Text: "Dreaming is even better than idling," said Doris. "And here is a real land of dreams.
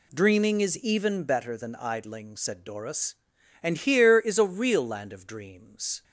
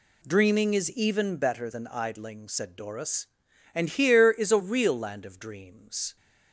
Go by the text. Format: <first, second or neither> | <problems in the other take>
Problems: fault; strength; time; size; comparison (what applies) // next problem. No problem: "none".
neither | none